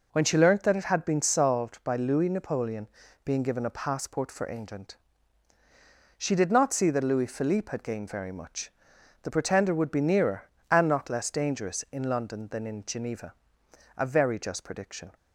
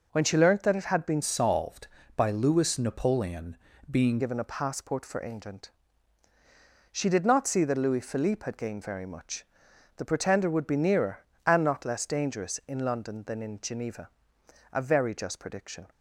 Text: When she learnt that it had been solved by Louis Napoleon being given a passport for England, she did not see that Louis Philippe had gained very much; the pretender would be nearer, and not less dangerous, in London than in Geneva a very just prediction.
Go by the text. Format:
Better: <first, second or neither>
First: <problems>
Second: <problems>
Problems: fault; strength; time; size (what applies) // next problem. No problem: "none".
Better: first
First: pauses between "Napoleon" and "being"; at 2.8 s; 0.38 s long // pauses between "Geneva" and "a"; noticeable; at 13.3 s; 0.64 s long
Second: changes voice from "solved" to "being"; from 1.2 to 4.1 s; 2.9 s long // pauses between "Napoleon" and "being"; slight; at 3.5 s; 0.32 s long // pauses between "Geneva" and "a"; noticeable; at 14.0 s; 0.64 s long